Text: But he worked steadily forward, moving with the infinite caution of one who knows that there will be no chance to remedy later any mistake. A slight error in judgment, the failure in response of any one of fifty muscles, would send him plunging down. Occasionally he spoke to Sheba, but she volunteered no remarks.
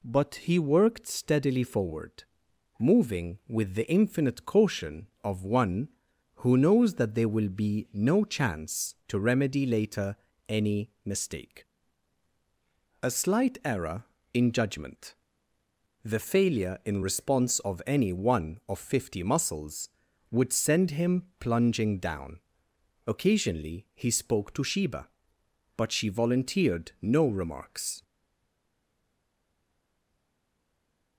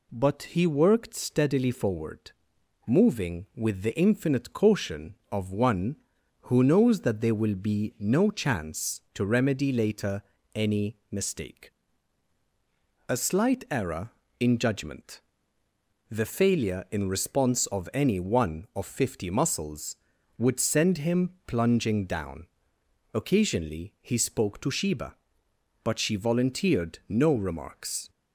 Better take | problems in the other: second | pauses between "later" and "any"; slight; at 10.1 s; 0.32 s long; slight in the second // pauses between "him" and "plunging"; slight; at 21.2 s; 0.16 s long; slight in the second // stays silent after the last word; strong; from 28.0 s on; 3.1 s long

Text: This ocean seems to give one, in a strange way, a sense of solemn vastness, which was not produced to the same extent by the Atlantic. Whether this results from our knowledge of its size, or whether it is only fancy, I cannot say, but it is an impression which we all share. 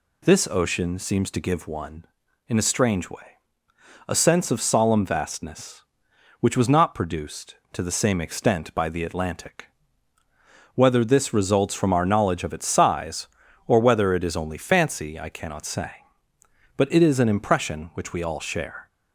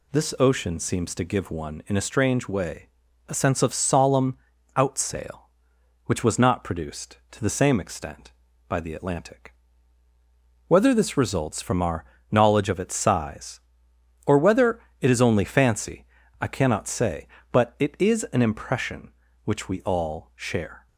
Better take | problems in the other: first | says "outsail" for "vastness"; at 4.7 s // pauses between "our" and "knowledge"; slight; at 12.0 s; 0.26 s long // pauses between "whether" and "it"; slight; at 14.7 s; 0.20 s long

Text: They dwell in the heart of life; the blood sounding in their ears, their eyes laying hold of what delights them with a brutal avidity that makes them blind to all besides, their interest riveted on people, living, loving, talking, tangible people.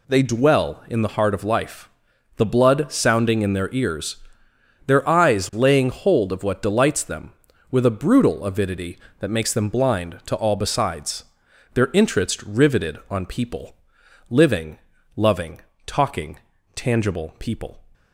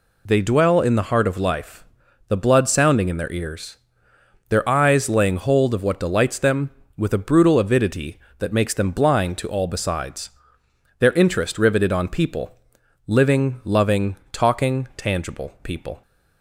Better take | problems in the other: neither | none

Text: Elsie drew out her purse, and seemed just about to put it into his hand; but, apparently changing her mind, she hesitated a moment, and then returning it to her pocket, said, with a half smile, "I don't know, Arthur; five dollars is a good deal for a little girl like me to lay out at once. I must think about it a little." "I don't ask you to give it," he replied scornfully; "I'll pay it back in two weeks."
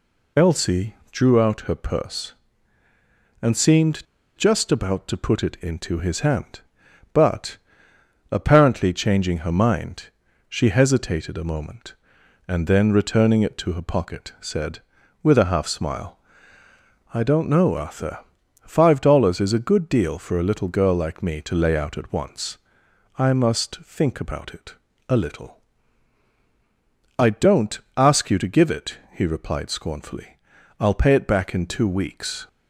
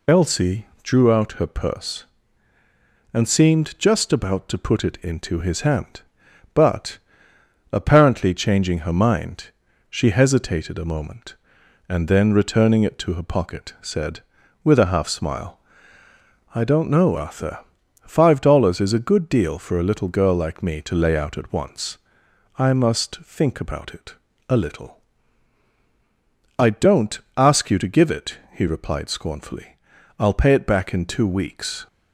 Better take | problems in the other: second | pauses between "Elsie" and "drew"; slight; at 0.9 s; 0.16 s long; slight in the second // pauses between "seemed" and "just"; slight; at 4.0 s; 0.31 s long // pauses between "it" and "a"; slight; at 24.7 s; 0.34 s long; slight in the second // pauses between "don't" and "ask"; slight; at 27.7 s; 0.18 s long; slight in the second

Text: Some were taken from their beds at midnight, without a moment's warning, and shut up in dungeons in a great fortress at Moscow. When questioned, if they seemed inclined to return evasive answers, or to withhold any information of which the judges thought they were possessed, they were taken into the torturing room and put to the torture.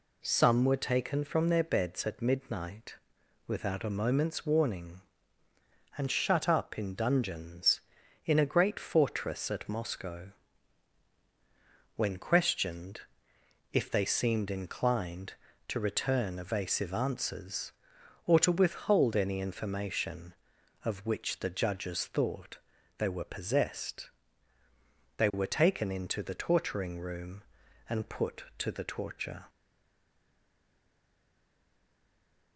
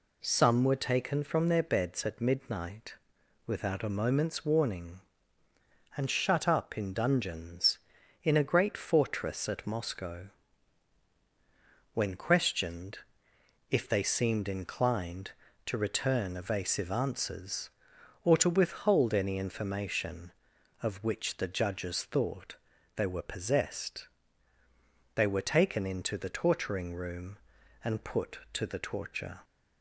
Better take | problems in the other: second | pauses between "thought" and "they"; at 22.5 s; 0.40 s long; also in the second // stays silent after the last word; strong; from 29.4 s on; 3.1 s long

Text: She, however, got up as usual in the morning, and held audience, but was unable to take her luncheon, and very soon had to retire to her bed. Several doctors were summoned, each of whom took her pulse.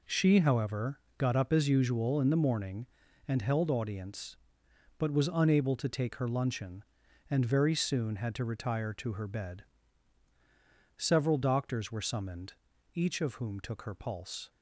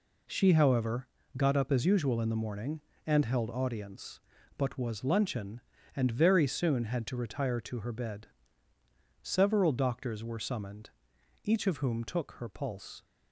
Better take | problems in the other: first | skips "unable to take her"; at 5.0 s

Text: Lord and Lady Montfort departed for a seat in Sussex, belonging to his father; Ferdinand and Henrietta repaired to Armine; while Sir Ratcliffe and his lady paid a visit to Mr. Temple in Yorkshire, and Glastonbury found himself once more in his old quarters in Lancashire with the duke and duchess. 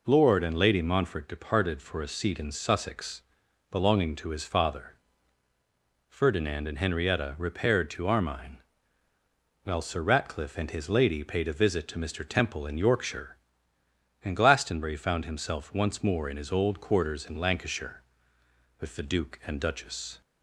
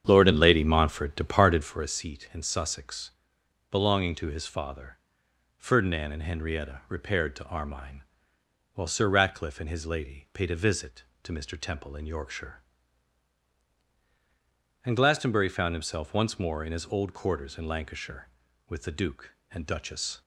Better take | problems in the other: first | starts louder than the rest; strong; until 1.9 s; 8.5 dB

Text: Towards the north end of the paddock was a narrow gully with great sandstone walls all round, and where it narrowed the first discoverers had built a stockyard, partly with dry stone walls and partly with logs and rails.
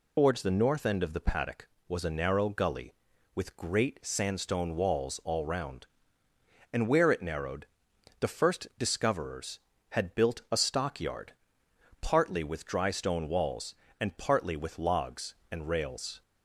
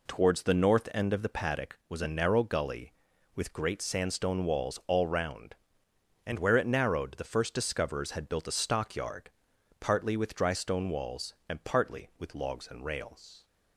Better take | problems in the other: second | loses the start of "Towards"; at 0.1 s; 95 ms // pauses between "narrowed" and "the"; noticeable; at 7.6 s; 0.54 s long

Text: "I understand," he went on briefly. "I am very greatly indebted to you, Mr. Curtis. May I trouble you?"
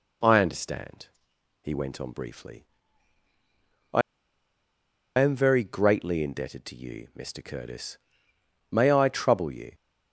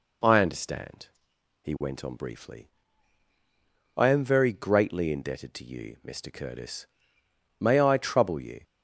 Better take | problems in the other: second | pauses between "I" and "am"; at 4.0 s; 1.1 s long

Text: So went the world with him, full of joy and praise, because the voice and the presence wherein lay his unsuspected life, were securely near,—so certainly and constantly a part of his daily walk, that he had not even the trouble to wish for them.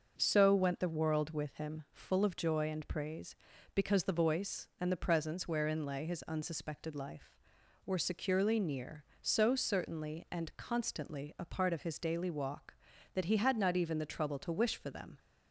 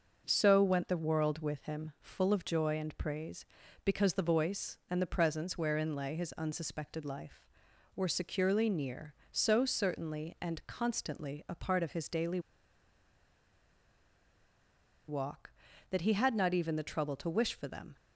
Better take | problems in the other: first | pauses between "daily" and "walk"; strong; at 12.3 s; 2.6 s long

